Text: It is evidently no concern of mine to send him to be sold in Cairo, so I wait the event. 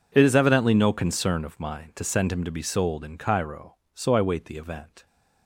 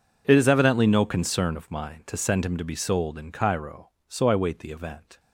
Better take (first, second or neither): neither